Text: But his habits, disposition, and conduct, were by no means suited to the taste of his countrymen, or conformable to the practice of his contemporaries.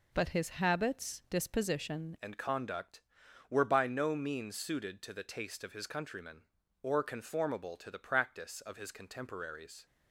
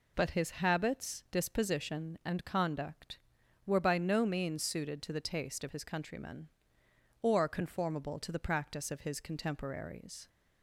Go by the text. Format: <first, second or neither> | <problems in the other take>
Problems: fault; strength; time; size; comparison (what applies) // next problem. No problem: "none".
second | changes voice at "and"; from 2.2 s on; 7.6 s long